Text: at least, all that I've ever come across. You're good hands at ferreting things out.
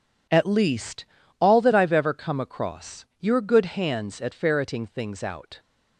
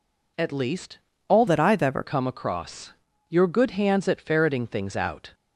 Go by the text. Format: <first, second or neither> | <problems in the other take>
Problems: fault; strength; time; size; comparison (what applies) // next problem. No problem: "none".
first | changes voice from "that" to "ever"; from 1.4 to 2.0 s; 0.6 s long